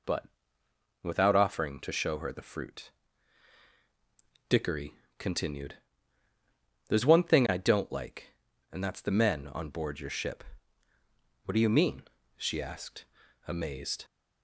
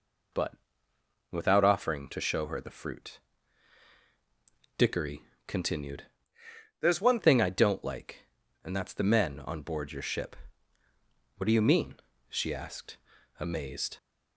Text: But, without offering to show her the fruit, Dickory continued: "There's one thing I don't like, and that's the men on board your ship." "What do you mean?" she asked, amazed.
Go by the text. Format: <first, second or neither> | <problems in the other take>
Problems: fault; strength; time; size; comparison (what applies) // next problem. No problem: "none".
first | pauses between "Dickory" and "continued"; slight; at 5.2 s; 0.24 s long; slight in the first // changes voice from "There's" to "one"; from 6.7 to 7.1 s; 0.4 s long